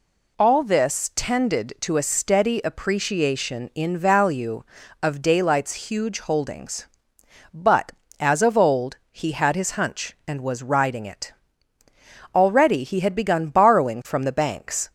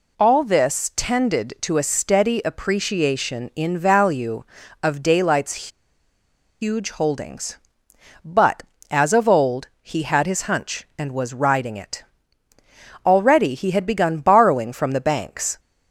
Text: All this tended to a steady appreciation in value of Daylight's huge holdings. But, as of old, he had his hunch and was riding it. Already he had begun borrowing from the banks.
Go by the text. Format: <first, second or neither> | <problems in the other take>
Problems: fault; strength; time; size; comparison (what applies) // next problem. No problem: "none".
first | pauses between "Daylight's" and "huge"; noticeable; at 5.6 s; 0.92 s long